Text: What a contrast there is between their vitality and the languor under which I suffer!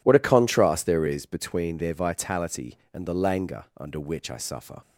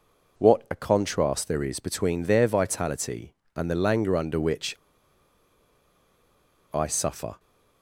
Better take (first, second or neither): first